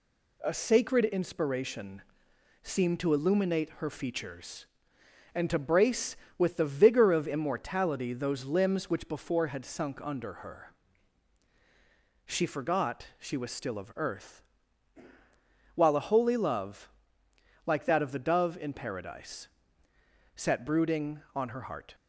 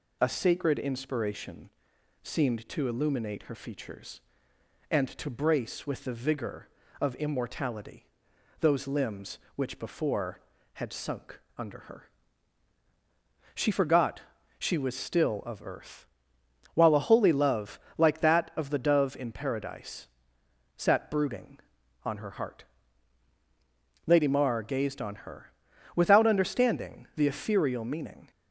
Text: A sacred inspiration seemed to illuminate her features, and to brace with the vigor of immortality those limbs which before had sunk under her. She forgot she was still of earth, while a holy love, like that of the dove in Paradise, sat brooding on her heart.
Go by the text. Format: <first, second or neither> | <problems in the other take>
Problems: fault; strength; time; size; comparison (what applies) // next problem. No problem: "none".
first | pauses between "inspiration" and "seemed"; noticeable; at 1.6 s; 0.54 s long; noticeable in the first // pauses between "immortality" and "those"; noticeable; at 8.0 s; 0.54 s long // pauses between "sunk" and "under"; slight; at 11.3 s; 0.18 s long // pauses between "forgot" and "she"; slight; at 14.2 s; 0.36 s long // goes on to say "Lady Mar gazed on her without understanding the ethereal meaning"; strong; from 24.0 s on; 4.2 s long